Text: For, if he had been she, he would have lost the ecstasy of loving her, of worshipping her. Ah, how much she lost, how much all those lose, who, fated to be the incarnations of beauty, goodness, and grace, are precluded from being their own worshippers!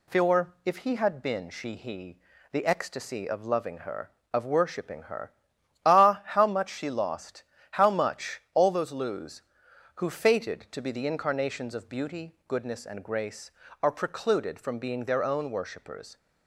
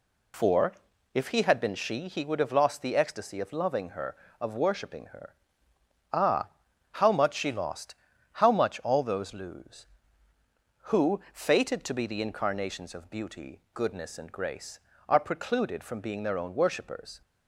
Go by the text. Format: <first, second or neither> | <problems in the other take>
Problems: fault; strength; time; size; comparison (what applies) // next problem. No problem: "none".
second | skips "would have lost"; at 2.3 s